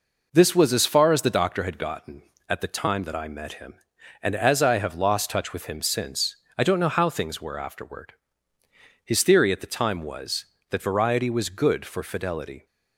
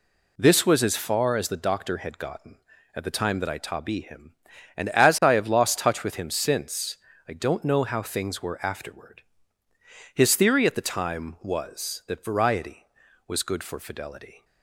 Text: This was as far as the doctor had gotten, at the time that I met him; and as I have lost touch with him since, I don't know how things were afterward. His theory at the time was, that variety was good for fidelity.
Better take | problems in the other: first | says "tabi" for "met"; at 3.5 s

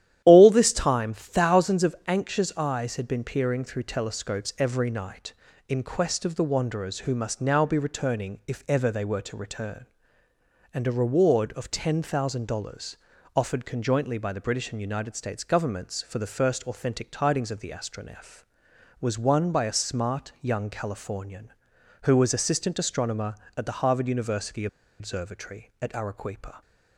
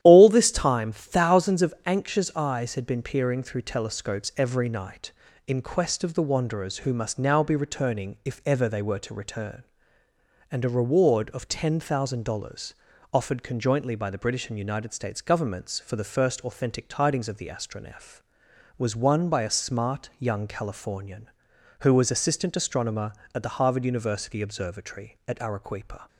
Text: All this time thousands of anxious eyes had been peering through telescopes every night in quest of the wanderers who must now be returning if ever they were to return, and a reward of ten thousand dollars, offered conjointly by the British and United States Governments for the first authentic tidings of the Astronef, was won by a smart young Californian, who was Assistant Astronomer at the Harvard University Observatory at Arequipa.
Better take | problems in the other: second | starts louder than the rest; strong; until 1.2 s; 11.5 dB; strong in the second // pauses between "University" and "Observatory"; slight; at 24.6 s; 0.33 s long

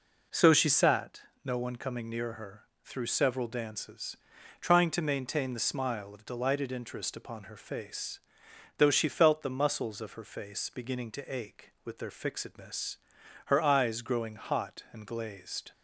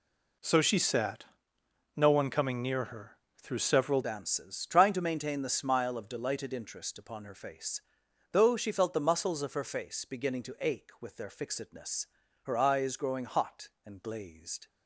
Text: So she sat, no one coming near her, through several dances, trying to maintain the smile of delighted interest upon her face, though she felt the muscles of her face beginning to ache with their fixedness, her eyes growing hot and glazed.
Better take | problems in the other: first | changes voice at "dances"; from 4.0 s on; 10.6 s long

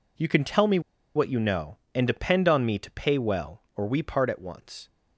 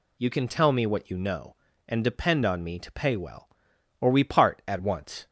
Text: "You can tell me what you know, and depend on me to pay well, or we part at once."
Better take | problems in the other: second | pauses between "me" and "what"; slight; at 0.7 s; 0.35 s long

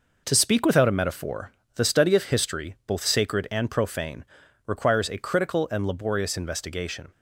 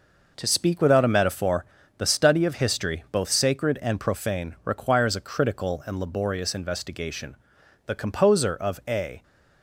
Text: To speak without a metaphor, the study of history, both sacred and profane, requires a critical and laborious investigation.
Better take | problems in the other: first | goes on to say "The composer of a"; from 7.8 s on; 1.3 s long

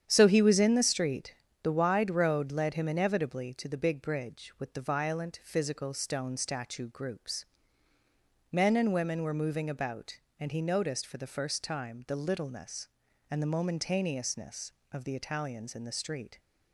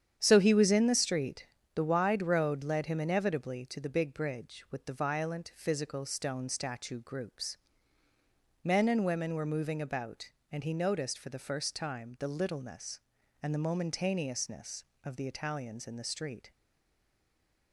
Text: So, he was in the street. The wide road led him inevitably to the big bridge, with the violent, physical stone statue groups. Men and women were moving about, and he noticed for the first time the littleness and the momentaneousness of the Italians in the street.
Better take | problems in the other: first | starts louder than the rest; strong; until 1.1 s; 9 dB; strong in the first // stays silent after the last word; noticeable; from 16.5 s on; 1.2 s long

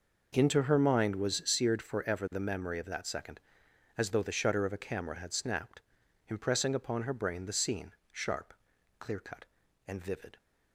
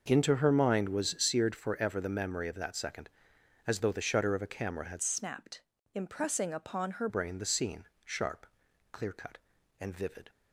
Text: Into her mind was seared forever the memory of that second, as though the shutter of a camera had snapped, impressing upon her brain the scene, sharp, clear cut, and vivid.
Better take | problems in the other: first | changes voice from "snapped" to "her"; from 5.0 to 7.0 s; 2.0 s long

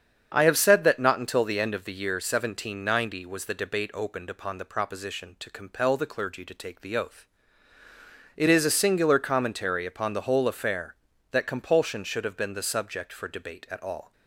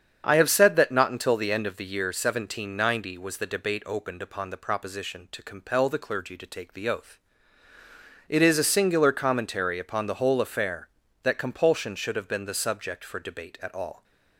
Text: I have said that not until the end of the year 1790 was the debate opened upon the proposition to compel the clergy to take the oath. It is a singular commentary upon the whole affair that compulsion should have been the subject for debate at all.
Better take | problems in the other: neither | starts louder than the rest; strong; the same in both

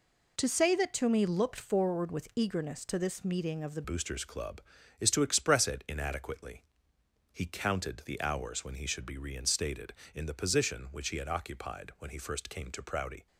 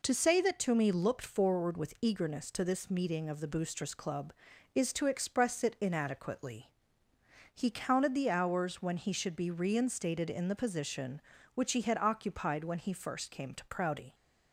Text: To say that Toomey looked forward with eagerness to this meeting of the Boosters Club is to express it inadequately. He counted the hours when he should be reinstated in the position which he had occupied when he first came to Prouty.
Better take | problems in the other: second | changes voice at "Boosters"; from 3.8 s on; 9.4 s long

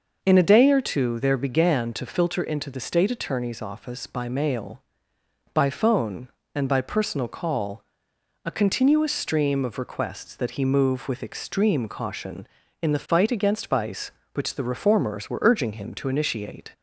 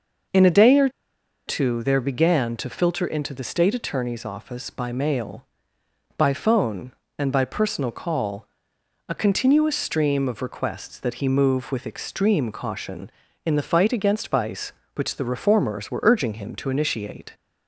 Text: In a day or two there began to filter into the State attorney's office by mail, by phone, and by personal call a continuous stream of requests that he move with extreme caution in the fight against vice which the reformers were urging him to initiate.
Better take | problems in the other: first | pauses between "or" and "two"; noticeable; at 0.8 s; 0.58 s long // pauses between "call" and "a"; noticeable; at 8.4 s; 0.62 s long; noticeable in the first

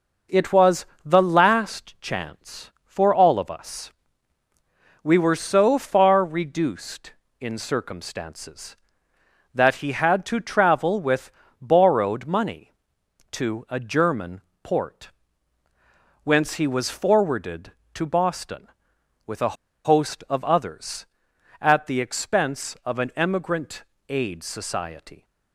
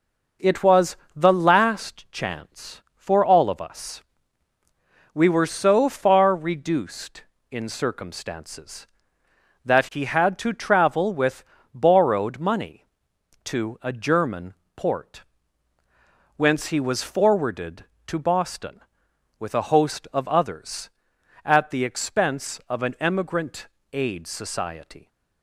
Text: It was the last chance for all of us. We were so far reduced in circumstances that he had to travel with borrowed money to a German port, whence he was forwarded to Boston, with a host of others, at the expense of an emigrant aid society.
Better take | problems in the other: second | pauses between "was" and "the"; slight; at 0.8 s; 0.18 s long; slight in the second // pauses between "with" and "borrowed"; slight; at 11.3 s; 0.28 s long; slight in the second // pauses between "German" and "port"; slight; at 14.4 s; 0.20 s long; slight in the second // pauses between "a" and "host"; slight; at 19.5 s; 0.30 s long // pauses between "emigrant" and "aid"; slight; at 23.8 s; 0.24 s long; slight in the second

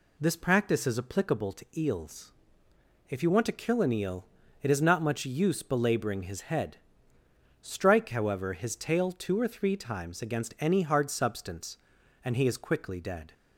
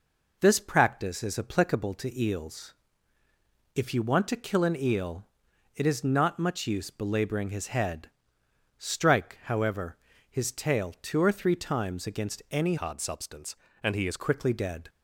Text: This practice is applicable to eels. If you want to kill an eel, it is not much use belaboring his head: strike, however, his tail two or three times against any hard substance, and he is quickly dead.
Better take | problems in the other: first | changes voice from "hard" to "is"; from 12.7 to 14.1 s; 1.4 s long

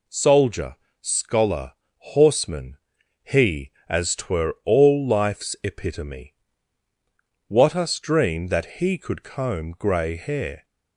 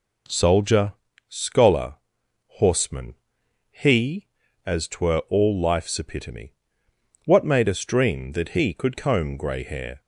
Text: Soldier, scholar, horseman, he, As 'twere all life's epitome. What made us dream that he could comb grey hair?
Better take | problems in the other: second | skips "made"; at 7.7 s

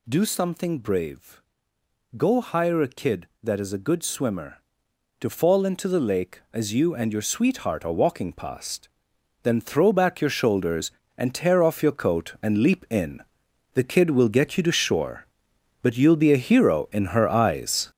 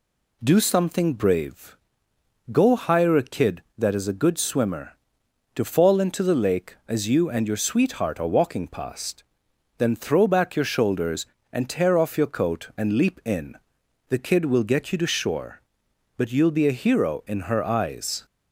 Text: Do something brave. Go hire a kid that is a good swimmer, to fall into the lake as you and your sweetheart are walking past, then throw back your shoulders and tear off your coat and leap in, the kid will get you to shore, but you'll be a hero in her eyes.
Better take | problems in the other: second | gets louder; strong; throughout; 7.5 dB

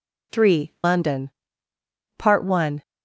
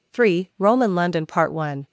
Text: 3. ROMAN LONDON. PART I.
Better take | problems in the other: second | skips "ROMAN"; at 0.7 s

